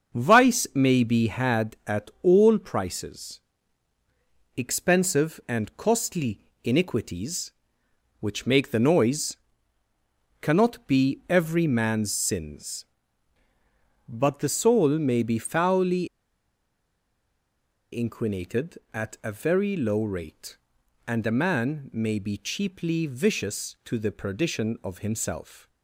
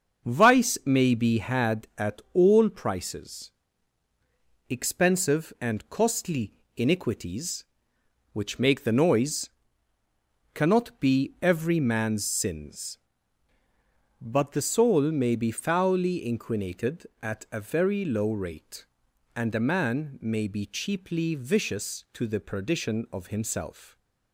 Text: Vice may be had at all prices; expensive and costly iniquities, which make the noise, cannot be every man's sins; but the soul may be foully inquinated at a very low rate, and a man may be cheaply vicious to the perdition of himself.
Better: second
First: starts louder than the rest; until 1.2 s; 6.5 dB // pauses between "costly" and "iniquities"; slight; at 6.4 s; 0.22 s long // pauses between "foully" and "inquinated"; strong; at 16.0 s; 1.8 s long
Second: starts louder than the rest; until 1.3 s; 6.5 dB // pauses between "costly" and "iniquities"; slight; at 6.5 s; 0.22 s long

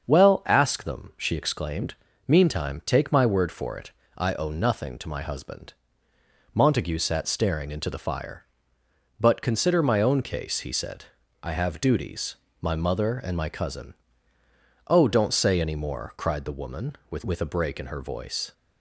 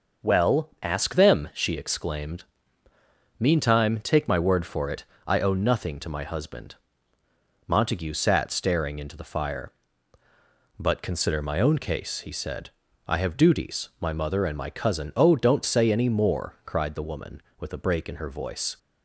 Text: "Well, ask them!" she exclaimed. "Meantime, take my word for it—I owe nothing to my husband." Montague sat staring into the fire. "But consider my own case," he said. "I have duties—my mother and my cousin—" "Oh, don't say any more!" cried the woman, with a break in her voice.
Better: second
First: starts louder than the rest; until 1.0 s; 6.5 dB // says "with" twice; at 17.2 s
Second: starts louder than the rest; noticeable; until 1.3 s; 6 dB

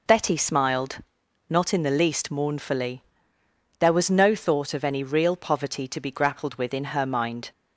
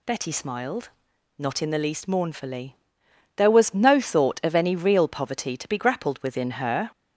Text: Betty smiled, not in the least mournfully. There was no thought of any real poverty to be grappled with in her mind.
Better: first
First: none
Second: stops before "mind"; at 6.9 s

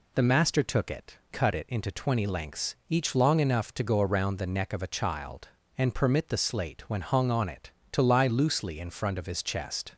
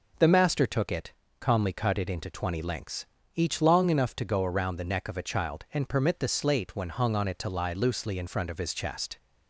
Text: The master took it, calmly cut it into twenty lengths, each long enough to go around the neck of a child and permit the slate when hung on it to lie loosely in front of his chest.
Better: second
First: skips "calmly"; at 1.2 s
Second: none

